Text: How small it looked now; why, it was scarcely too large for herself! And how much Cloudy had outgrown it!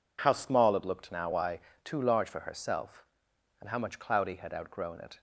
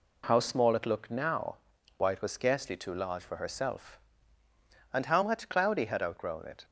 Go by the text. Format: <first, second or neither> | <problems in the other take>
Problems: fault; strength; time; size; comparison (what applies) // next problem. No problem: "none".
second | skips "it was scarcely"; at 1.7 s